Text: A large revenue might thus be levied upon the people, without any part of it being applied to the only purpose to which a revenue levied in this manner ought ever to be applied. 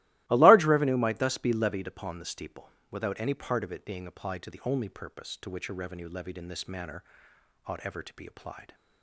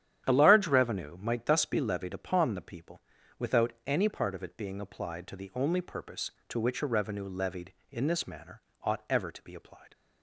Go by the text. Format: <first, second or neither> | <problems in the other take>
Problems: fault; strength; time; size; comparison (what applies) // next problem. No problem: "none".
second | starts louder than the rest; strong; until 1.2 s; 16.5 dB; strong in the second // says "steeple" for "people"; at 2.2 s // pauses between "manner" and "ought"; noticeable; at 7.0 s; 0.62 s long; slight in the second